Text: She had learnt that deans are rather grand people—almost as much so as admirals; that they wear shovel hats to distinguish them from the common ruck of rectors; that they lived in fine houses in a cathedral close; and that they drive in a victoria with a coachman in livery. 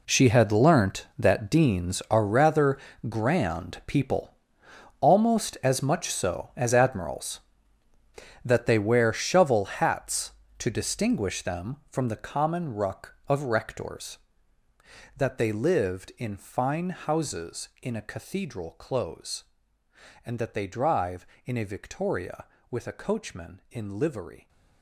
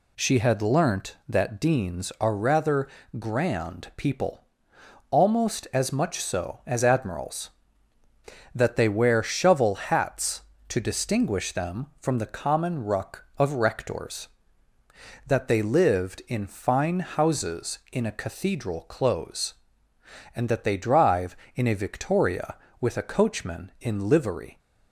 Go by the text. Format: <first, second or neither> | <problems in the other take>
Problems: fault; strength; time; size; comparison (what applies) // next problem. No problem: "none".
second | gets quieter; strong; throughout; 13.5 dB // pauses between "rather" and "grand"; slight; at 2.7 s; 0.30 s long; slight in the second